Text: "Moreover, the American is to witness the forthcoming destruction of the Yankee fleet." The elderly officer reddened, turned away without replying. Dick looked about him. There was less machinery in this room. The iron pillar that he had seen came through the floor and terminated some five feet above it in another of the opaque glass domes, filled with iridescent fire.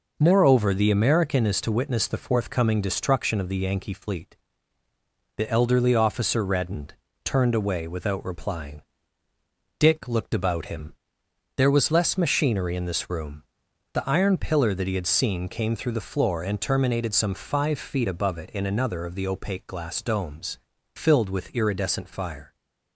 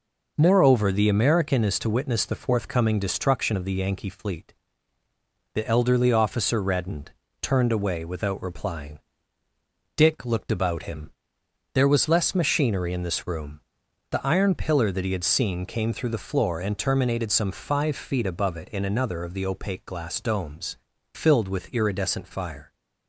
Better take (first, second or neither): neither